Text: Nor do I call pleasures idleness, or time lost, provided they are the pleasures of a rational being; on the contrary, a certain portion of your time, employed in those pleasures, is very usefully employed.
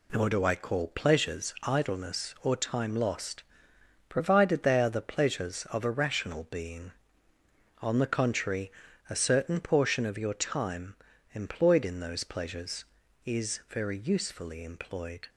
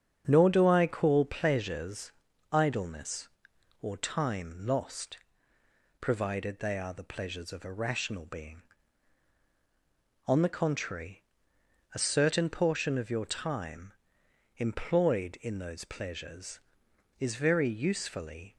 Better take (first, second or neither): first